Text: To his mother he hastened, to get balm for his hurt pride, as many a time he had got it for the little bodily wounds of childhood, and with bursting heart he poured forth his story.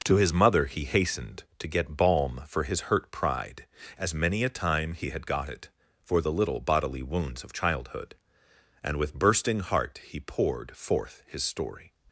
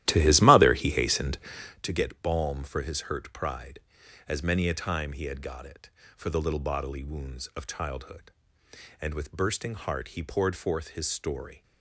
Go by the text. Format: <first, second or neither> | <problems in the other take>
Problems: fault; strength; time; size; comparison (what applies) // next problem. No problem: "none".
first | starts louder than the rest; strong; until 1.9 s; 14 dB